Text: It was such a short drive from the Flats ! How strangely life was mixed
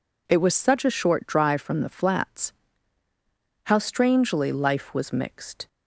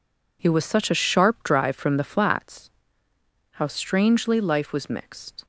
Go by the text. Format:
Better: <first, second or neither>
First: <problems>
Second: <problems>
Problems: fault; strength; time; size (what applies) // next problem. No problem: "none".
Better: first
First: none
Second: says "sharp" for "short"; at 1.0 s